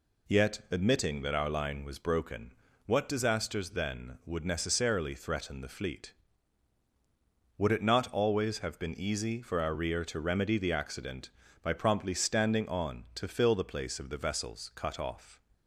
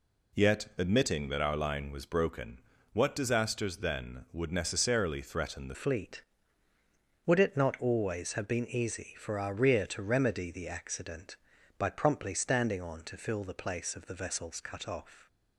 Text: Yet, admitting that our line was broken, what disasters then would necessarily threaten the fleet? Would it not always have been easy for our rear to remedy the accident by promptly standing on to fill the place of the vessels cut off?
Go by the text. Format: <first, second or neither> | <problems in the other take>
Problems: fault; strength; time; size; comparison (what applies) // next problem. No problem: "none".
first | changes voice at "fleet"; from 5.7 s on; 9.5 s long